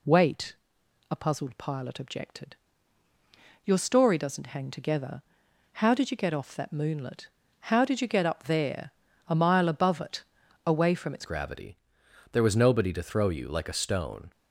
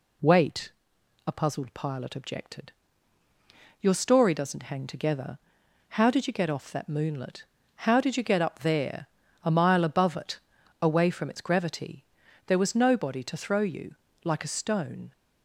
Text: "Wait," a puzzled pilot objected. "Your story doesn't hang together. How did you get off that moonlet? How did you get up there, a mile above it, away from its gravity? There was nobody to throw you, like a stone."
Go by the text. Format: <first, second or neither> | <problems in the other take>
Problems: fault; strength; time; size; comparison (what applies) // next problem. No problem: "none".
second | changes voice at "gravity"; from 11.2 s on; 3.1 s long